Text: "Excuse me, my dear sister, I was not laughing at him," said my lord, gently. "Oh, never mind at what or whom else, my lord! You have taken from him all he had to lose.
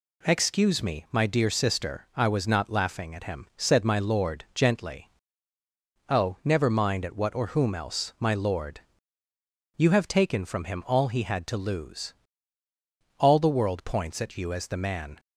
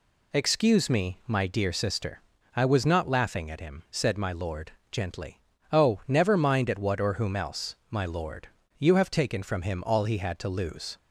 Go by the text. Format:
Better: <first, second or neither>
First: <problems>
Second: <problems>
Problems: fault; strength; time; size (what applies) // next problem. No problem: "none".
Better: second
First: goes on to say "All the world points at you as the man"; strong; from 13.1 s on; 2.0 s long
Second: none